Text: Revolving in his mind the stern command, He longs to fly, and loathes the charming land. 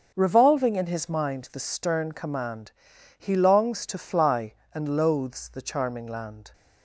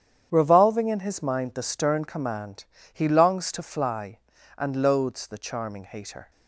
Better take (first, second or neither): first